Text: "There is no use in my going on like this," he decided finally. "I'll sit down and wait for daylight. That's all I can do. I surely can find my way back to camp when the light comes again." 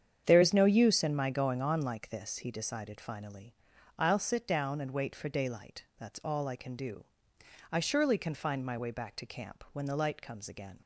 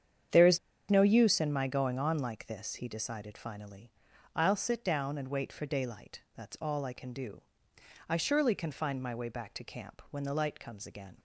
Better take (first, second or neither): first